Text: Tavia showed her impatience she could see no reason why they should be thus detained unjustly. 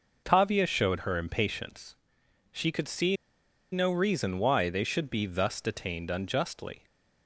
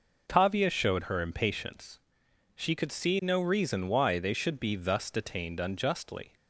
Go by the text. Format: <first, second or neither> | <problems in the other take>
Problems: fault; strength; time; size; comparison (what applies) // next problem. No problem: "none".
second | pauses between "impatience" and "she"; noticeable; at 1.9 s; 0.58 s long; noticeable in the second // pauses between "see" and "no"; noticeable; at 3.1 s; 0.56 s long